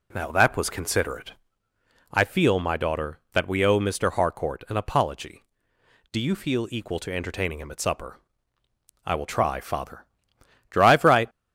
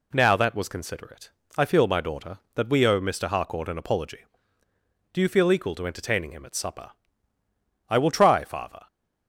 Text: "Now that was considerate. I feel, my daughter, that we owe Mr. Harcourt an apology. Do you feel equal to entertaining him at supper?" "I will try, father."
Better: second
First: goes on to say "Drive right"; from 10.7 s on; 0.58 s long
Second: none

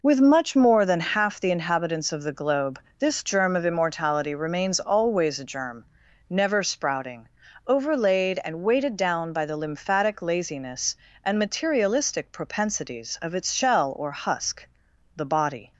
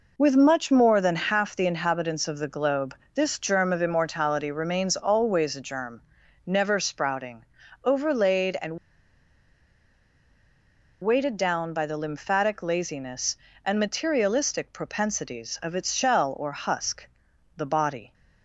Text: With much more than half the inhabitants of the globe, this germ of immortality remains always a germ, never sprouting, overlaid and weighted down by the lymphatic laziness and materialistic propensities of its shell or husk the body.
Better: first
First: pauses between "husk" and "the"; noticeable; at 14.6 s; 0.52 s long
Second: pauses between "and" and "weighted"; strong; at 8.7 s; 2.2 s long // pauses between "husk" and "the"; noticeable; at 17.0 s; 0.52 s long

